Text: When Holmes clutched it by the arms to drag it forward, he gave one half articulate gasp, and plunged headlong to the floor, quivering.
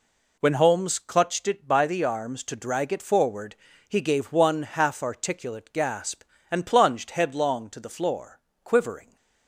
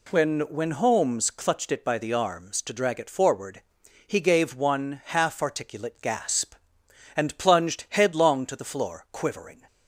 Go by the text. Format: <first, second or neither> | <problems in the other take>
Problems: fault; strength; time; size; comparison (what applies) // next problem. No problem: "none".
first | says "When" twice; at 0.4 s